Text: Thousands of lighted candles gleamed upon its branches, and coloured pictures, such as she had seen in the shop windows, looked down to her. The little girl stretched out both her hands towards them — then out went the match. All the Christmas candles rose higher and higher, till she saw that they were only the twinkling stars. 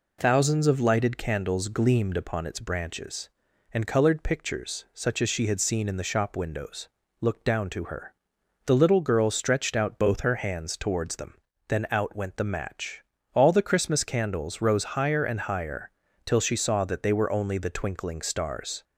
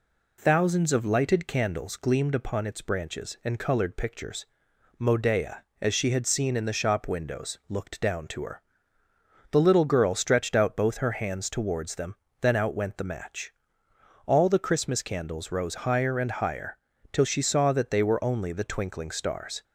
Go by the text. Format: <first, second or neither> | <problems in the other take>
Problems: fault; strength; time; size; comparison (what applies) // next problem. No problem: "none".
first | says "modea" for "such"; at 4.9 s